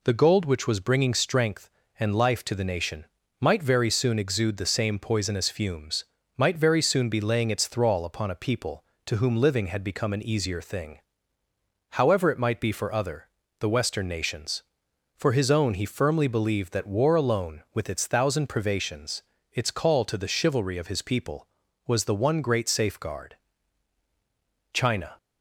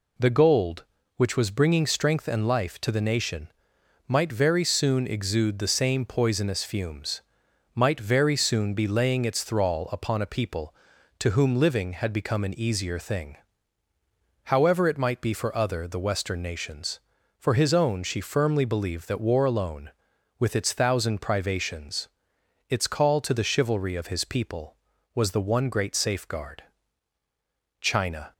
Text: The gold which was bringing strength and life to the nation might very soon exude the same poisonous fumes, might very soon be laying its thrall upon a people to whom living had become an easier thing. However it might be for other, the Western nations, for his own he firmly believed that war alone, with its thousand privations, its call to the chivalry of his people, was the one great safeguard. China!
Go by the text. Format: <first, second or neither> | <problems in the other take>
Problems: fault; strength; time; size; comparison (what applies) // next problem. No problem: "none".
first | pauses between "nation" and "might"; noticeable; at 3.5 s; 0.58 s long; slight in the first // says "she" for "he"; at 18.0 s